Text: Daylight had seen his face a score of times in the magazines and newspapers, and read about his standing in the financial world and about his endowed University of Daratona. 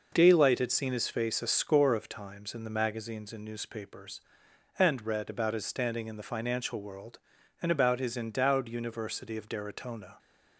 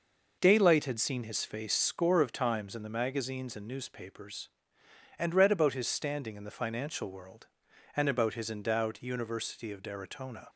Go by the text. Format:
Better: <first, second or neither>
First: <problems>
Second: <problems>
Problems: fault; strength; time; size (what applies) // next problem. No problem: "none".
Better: first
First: none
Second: skips "a"; at 1.7 s